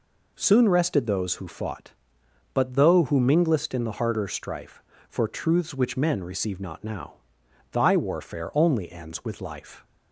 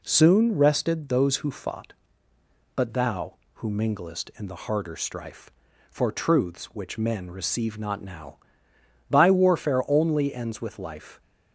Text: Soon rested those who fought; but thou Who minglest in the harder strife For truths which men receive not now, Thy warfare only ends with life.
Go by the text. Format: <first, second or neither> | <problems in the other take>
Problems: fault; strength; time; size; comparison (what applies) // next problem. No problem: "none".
second | says "though" for "thou"; at 2.7 s